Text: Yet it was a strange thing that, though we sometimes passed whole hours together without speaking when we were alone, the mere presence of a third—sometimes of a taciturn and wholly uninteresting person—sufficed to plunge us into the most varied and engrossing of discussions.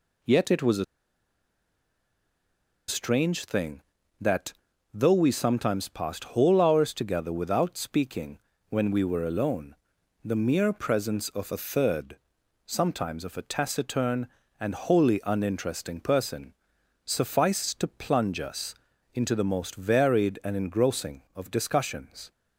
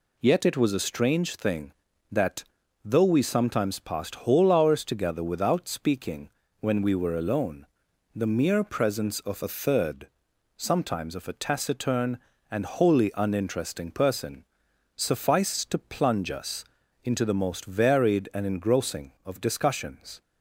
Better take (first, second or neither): second